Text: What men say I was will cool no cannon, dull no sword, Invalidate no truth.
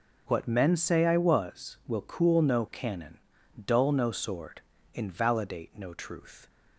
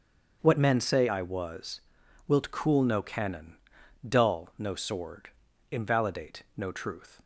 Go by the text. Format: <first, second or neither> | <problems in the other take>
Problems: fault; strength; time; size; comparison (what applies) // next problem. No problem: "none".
first | starts louder than the rest; until 1.4 s; 7 dB // says "wilt" for "will"; at 2.2 s